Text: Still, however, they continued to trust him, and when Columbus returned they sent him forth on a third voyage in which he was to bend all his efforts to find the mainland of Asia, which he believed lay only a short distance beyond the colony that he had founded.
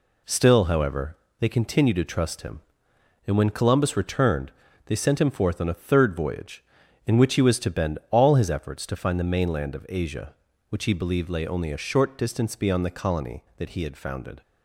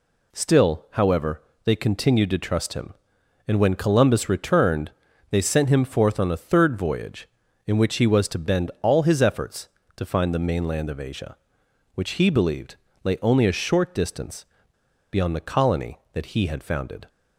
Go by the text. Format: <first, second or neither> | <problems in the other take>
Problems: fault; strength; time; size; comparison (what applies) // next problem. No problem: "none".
first | pauses between "returned" and "they"; at 4.9 s; 0.40 s long; slight in the first // pauses between "believed" and "lay"; slight; at 12.7 s; 0.28 s long // pauses between "distance" and "beyond"; noticeable; at 14.4 s; 0.66 s long